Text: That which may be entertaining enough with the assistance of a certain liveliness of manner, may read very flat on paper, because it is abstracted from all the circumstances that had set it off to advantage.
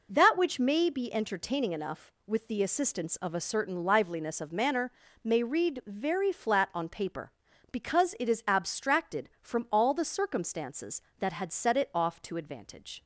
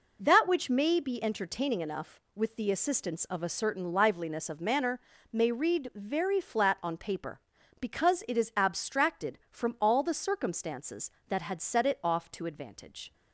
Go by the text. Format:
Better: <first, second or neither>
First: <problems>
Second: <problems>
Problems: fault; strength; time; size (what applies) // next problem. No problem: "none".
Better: neither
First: none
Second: none